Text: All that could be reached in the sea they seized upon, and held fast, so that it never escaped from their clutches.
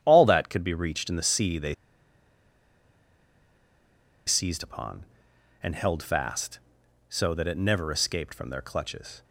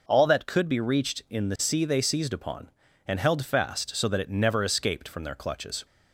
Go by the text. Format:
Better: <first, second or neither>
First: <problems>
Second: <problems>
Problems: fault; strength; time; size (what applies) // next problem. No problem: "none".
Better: second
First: starts louder than the rest; strong; until 1.0 s; 9.5 dB // pauses between "they" and "seized"; strong; at 1.7 s; 2.5 s long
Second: none